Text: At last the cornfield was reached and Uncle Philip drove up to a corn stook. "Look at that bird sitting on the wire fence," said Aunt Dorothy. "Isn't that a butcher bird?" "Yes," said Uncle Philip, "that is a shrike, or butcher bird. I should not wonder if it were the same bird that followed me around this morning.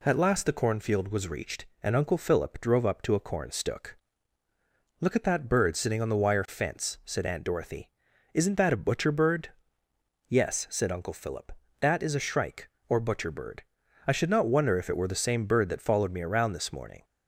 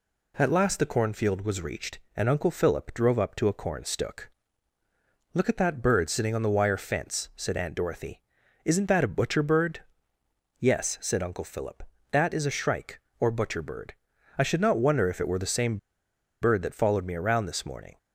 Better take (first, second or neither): first